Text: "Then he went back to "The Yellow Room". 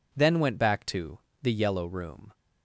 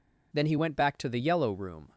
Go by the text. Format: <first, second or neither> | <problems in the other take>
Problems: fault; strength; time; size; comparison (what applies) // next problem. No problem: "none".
second | skips "he"; at 0.3 s // pauses between "to" and "The"; slight; at 1.1 s; 0.21 s long